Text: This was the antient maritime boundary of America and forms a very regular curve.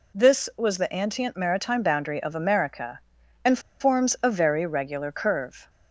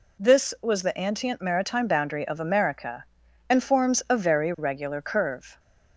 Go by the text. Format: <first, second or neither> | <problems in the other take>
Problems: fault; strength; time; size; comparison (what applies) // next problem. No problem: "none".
second | pauses between "and" and "forms"; slight; at 3.5 s; 0.21 s long